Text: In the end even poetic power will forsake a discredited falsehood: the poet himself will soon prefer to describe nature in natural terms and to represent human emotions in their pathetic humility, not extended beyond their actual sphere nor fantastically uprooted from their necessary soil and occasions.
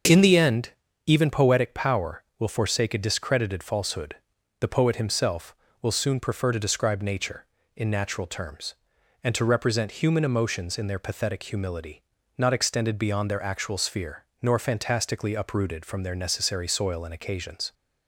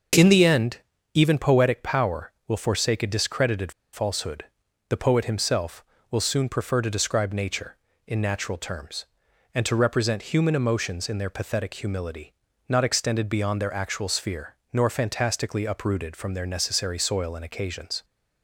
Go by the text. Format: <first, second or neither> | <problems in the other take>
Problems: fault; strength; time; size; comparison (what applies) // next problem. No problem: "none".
first | starts louder than the rest; until 1.5 s; 6.5 dB; also in the first // pauses between "end" and "even"; slight; at 0.7 s; 0.36 s long; slight in the first // pauses between "discredited" and "falsehood"; slight; at 3.7 s; 0.21 s long // pauses between "sphere" and "nor"; slight; at 14.5 s; 0.16 s long; slight in the first